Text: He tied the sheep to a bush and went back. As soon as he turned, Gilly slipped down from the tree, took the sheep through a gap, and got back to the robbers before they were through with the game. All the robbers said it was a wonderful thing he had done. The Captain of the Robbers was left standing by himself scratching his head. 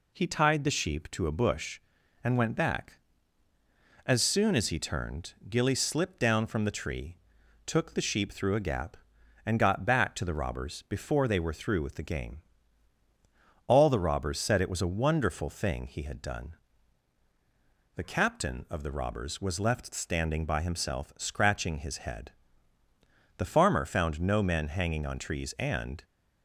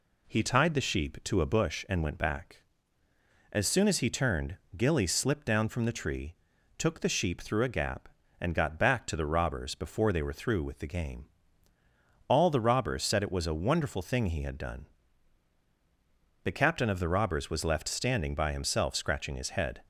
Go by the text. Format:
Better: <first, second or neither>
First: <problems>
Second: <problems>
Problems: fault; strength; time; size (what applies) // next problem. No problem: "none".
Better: second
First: goes on to say "The farmer found no men hanging on trees and"; strong; from 23.3 s on; 2.6 s long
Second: none